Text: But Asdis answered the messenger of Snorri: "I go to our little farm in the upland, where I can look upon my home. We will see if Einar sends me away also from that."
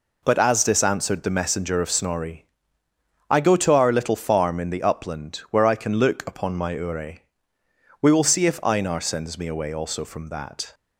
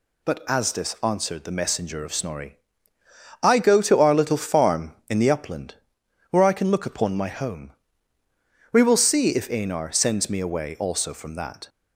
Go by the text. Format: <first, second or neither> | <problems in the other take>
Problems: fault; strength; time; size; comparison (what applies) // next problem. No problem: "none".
second | says "ure" for "home"; at 6.7 s